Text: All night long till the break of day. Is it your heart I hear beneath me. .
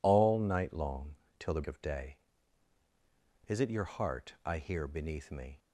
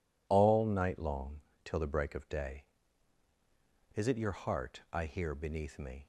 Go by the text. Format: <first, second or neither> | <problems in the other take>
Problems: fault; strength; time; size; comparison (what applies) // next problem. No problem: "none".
second | pauses between "long" and "till"; slight; at 1.1 s; 0.24 s long; slight in the second // skips "break"; at 1.6 s